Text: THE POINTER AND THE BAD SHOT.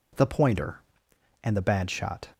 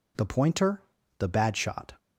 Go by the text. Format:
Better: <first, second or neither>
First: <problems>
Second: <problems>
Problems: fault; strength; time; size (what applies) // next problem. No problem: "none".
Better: first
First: none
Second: skips "AND"; at 1.0 s